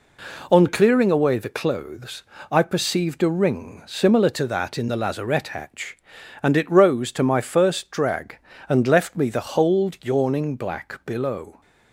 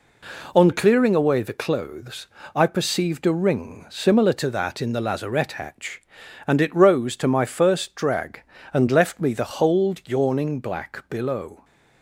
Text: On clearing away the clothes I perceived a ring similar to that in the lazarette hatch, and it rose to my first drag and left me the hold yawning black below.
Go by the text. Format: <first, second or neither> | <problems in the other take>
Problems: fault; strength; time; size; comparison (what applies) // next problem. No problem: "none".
neither | pauses between "clothes" and "I"; slight; the same in both